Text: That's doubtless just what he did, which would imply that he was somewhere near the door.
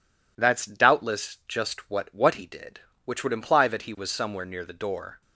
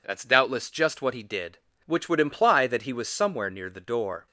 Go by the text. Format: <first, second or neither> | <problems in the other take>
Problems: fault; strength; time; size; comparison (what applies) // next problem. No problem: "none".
second | says "what" twice; at 2.1 s